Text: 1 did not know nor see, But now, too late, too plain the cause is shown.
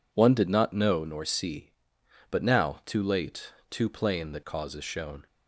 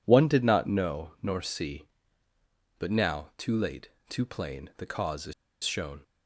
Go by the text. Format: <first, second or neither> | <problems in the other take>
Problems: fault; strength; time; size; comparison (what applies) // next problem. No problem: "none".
first | pauses between "is" and "shown"; slight; at 5.3 s; 0.31 s long